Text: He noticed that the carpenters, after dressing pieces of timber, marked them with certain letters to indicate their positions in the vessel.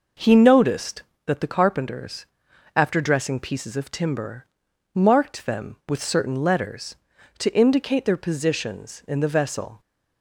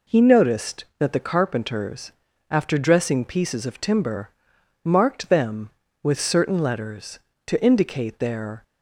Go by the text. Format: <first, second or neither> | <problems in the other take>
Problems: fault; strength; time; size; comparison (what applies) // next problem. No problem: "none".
first | stops before "positions in the vessel"; at 8.6 s